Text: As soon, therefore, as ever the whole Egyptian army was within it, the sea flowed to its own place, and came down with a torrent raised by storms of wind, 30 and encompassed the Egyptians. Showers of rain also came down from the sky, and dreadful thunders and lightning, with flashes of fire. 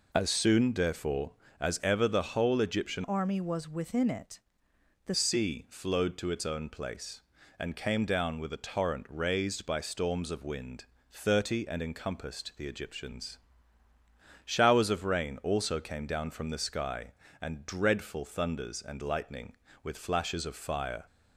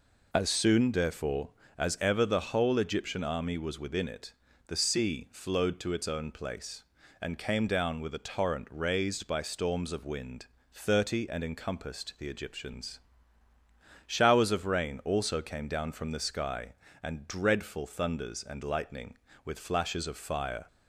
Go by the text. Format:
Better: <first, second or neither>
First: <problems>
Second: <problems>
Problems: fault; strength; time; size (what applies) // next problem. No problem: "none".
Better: second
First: changes voice from "army" to "the"; from 3.0 to 5.1 s; 2.1 s long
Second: none